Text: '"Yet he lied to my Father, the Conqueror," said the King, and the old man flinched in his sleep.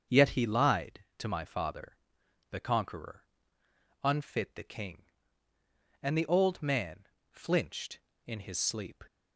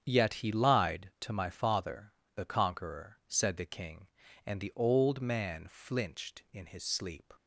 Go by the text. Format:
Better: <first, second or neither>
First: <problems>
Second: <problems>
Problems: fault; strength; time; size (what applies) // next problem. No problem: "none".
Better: second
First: starts louder than the rest; until 1.2 s; 6.5 dB // says "unfit" for "said"; at 4.0 s // pauses between "man" and "flinched"; slight; at 7.0 s; 0.26 s long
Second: starts louder than the rest; strong; until 1.0 s; 8 dB